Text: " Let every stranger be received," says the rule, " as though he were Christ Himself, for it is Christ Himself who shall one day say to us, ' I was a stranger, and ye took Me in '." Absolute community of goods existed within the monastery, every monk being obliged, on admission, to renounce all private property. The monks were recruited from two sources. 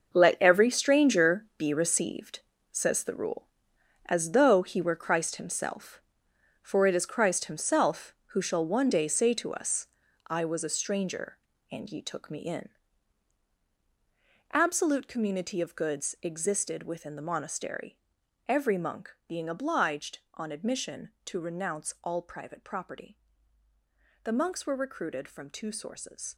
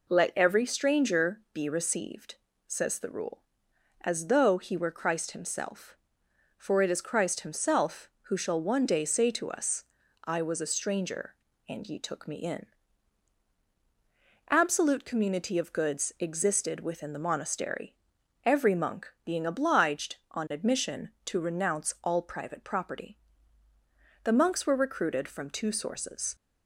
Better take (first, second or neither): second